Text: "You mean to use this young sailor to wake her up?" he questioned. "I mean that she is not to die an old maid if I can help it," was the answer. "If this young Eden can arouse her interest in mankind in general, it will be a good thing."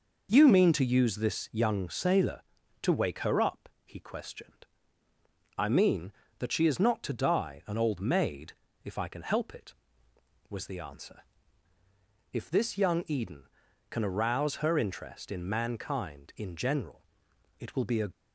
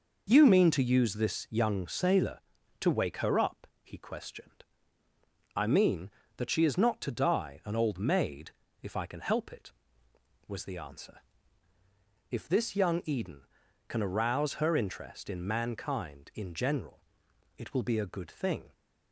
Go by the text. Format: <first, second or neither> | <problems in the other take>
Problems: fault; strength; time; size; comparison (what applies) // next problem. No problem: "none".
second | pauses between "maid" and "if"; slight; at 8.5 s; 0.32 s long; slight in the second // stops before "good thing"; at 18.1 s